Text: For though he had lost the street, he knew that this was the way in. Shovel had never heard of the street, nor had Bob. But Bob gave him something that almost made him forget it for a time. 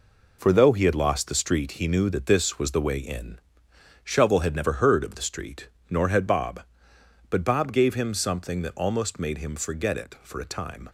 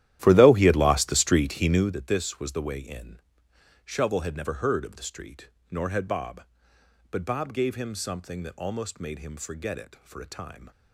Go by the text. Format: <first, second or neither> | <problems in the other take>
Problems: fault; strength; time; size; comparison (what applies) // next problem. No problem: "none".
first | starts louder than the rest; strong; until 1.9 s; 13 dB